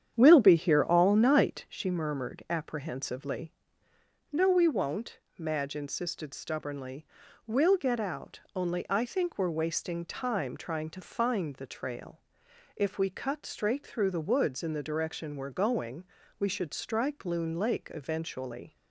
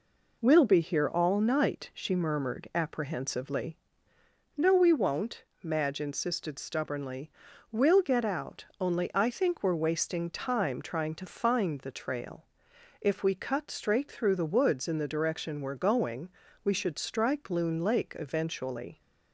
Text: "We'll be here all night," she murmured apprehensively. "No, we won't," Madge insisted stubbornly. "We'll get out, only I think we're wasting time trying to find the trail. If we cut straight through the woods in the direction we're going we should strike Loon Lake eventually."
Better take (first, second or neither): second